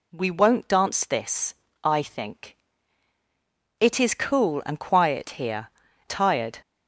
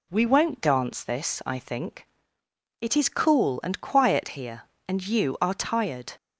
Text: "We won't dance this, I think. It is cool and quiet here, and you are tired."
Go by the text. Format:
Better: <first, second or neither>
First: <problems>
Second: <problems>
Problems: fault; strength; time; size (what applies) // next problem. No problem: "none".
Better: second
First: skips "and you are"; at 5.8 s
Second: none